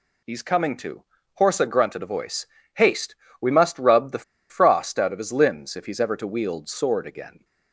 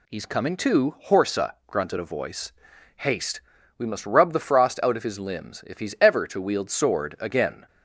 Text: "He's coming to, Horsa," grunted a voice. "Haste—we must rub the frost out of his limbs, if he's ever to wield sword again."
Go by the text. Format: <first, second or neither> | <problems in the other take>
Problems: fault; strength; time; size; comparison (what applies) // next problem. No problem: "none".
second | pauses between "the" and "frost"; slight; at 4.2 s; 0.26 s long